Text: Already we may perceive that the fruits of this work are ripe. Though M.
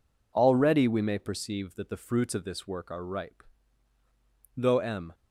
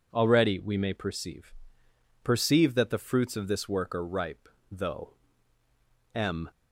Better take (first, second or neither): first